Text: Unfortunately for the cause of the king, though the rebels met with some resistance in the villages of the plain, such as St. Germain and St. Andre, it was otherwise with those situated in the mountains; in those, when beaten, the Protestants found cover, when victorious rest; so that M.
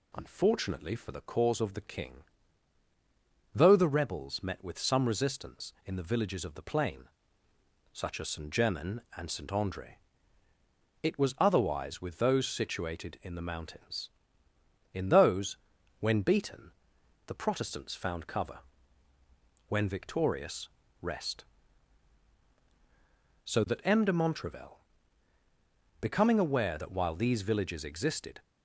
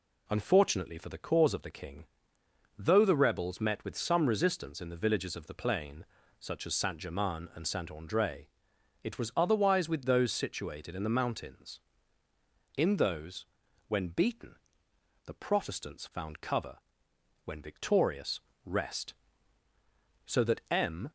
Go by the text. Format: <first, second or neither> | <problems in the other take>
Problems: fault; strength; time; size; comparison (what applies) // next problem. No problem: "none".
second | pauses between "victorious" and "rest"; slight; at 20.6 s; 0.32 s long; slight in the second // goes on to say "de Montrevel becoming aware that while these villages existed"; strong; from 24.0 s on; 4.3 s long